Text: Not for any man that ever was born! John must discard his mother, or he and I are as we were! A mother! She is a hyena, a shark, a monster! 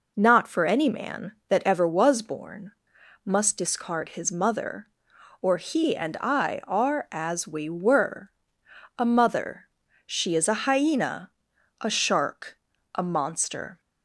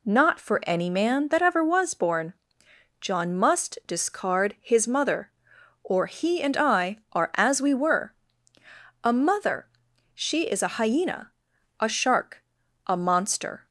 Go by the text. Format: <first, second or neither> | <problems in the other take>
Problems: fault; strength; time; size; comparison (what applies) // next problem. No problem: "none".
second | skips "John"; at 2.9 s